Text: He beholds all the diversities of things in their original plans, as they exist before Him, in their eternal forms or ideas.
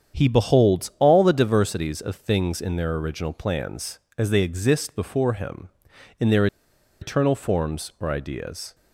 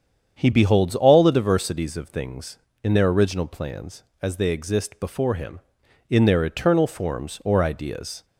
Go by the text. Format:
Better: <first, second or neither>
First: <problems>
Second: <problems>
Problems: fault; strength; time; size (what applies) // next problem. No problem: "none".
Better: second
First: starts louder than the rest; strong; until 1.2 s; 8 dB // pauses between "their" and "eternal"; noticeable; at 6.4 s; 0.54 s long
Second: starts louder than the rest; strong; until 1.4 s; 8 dB